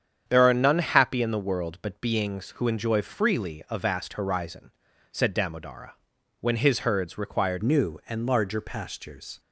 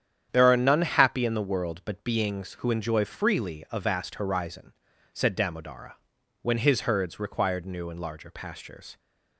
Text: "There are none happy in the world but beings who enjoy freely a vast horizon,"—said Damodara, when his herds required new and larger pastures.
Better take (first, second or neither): second